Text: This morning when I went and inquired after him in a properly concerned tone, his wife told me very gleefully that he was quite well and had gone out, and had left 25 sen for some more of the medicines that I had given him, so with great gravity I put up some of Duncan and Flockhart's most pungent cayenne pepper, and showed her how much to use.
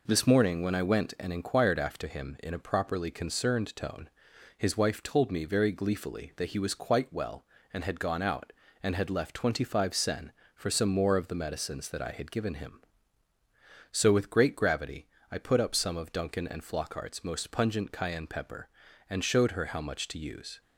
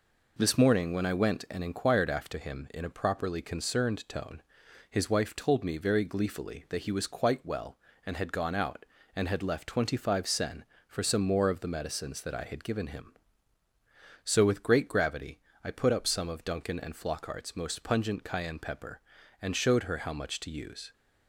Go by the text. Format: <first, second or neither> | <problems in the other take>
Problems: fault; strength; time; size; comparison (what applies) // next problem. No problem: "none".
neither | pauses between "gravity" and "I"; slight; the same in both